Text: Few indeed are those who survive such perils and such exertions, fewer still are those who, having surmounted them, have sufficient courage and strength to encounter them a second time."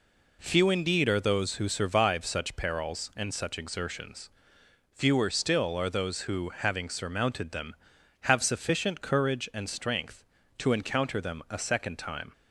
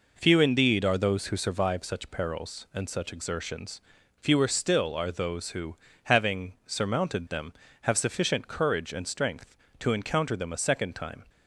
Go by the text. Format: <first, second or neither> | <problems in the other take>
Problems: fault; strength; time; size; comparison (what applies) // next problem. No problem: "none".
neither | none